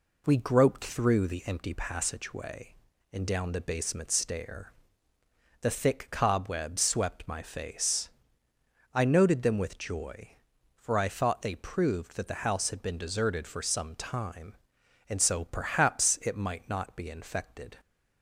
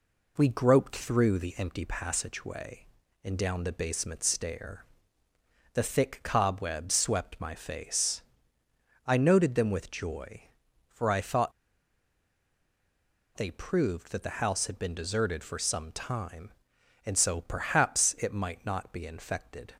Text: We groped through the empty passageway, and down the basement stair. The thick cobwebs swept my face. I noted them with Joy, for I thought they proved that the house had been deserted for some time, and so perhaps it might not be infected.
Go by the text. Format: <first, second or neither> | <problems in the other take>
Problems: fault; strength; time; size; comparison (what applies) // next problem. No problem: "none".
first | pauses between "thought" and "they"; strong; at 11.5 s; 1.8 s long